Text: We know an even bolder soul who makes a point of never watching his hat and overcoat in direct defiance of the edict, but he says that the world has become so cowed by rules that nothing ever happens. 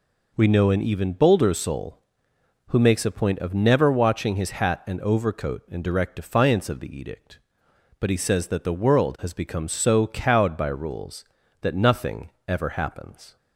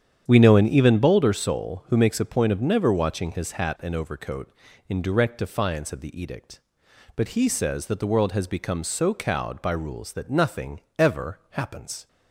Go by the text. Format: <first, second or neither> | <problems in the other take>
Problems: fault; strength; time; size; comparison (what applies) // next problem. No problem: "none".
first | starts louder than the rest; strong; until 1.3 s; 9 dB // pauses between "nothing" and "ever"; slight; at 10.8 s; 0.16 s long; slight in the first